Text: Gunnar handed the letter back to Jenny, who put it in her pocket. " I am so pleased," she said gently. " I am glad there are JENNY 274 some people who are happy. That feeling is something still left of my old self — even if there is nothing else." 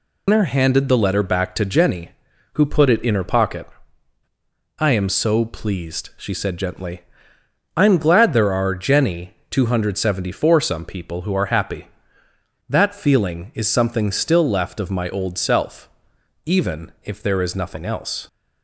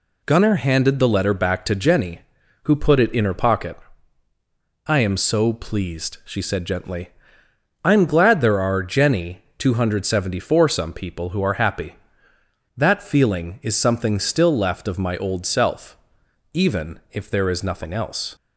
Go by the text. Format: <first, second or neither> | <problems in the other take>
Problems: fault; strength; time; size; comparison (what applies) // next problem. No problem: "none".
second | loses the start of "Gunnar"; at 0.2 s; 145 ms